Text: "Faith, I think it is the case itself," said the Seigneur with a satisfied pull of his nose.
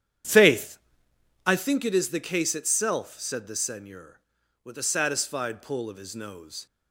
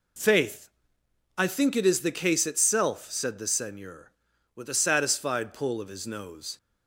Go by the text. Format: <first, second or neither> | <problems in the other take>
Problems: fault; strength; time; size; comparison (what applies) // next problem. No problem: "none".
second | starts louder than the rest; strong; until 1.7 s; 9.5 dB